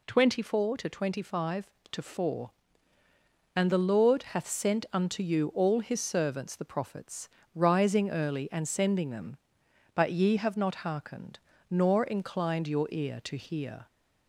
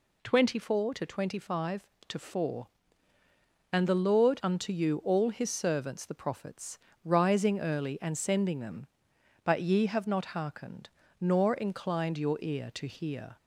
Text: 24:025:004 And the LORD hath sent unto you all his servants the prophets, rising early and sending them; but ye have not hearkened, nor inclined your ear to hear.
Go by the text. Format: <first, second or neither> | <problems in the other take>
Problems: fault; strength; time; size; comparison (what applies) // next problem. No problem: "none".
first | skips "hath sent"; at 4.4 s